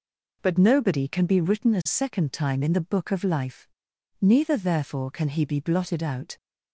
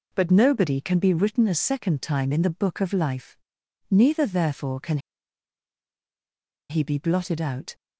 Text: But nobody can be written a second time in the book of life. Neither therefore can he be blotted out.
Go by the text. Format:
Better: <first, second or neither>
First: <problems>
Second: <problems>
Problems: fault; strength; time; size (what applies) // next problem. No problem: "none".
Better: first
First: none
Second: pauses between "can" and "he"; strong; at 4.9 s; 1.7 s long